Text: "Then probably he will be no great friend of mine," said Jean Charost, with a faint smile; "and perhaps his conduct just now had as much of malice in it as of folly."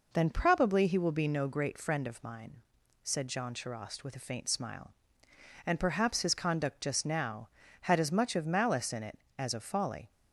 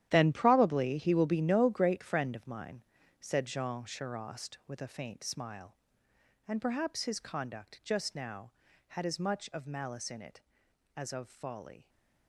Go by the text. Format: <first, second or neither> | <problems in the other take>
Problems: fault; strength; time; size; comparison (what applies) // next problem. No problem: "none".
first | gets quieter; strong; throughout; 13 dB